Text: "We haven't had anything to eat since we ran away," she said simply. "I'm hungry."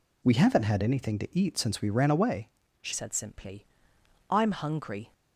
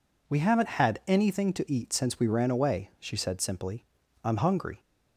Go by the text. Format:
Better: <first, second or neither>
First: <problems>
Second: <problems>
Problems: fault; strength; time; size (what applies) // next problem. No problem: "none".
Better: second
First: changes voice at "said"; from 2.9 s on; 2.2 s long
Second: none